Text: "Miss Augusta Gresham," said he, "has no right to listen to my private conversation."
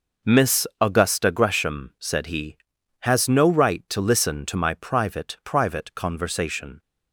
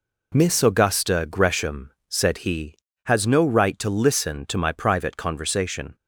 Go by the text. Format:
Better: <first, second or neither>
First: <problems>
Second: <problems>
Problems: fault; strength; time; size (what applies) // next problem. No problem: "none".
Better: second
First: says "private" twice; at 5.4 s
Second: none